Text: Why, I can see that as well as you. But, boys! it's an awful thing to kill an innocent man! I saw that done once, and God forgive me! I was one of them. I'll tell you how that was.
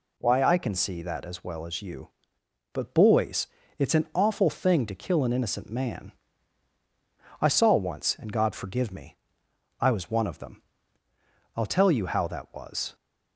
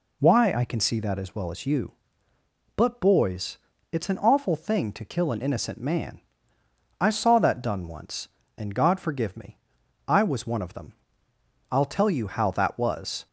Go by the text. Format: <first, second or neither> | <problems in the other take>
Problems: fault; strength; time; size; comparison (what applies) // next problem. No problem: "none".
second | skips "that done"; at 7.7 s